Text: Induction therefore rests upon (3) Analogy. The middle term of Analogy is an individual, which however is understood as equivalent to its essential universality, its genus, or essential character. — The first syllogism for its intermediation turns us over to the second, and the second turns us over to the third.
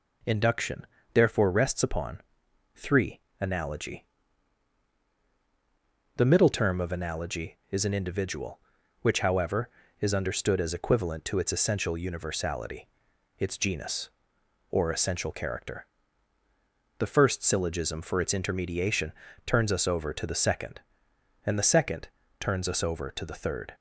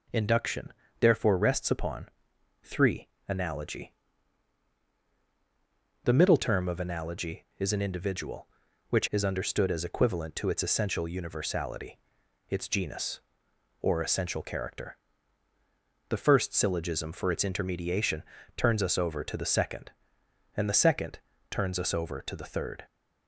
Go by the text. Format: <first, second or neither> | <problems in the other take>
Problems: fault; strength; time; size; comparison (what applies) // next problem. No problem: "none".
first | pauses between "Induction" and "therefore"; slight; at 0.7 s; 0.30 s long; slight in the first // skips "however"; at 9.0 s // pauses between "intermediation" and "turns"; slight; at 18.2 s; 0.32 s long; slight in the first // pauses between "second" and "turns"; slight; at 21.2 s; 0.30 s long; slight in the first